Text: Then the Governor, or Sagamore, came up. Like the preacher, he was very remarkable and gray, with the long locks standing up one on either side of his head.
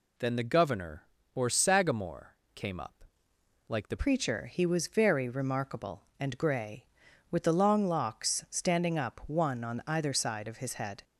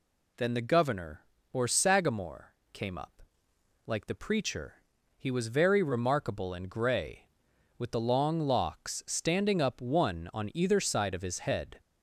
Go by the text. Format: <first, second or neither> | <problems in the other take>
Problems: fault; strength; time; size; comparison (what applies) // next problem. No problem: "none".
second | changes voice at "preacher"; from 3.9 s on; 7.1 s long